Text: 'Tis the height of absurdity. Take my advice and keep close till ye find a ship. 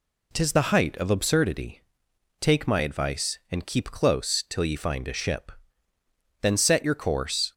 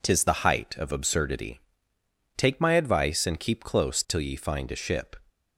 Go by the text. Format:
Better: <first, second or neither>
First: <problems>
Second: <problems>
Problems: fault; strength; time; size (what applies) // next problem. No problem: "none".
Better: second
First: goes on to say "Then set your course"; noticeable; from 6.4 s on; 1.1 s long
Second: none